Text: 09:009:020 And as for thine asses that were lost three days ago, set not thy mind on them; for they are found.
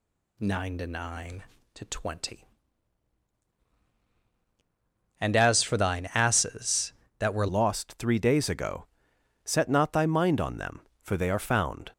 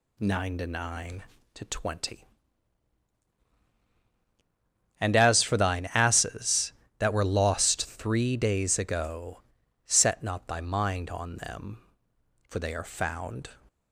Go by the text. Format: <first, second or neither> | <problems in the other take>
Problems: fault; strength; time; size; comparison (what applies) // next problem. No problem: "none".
second | changes voice at "lost"; from 7.4 s on; 4.5 s long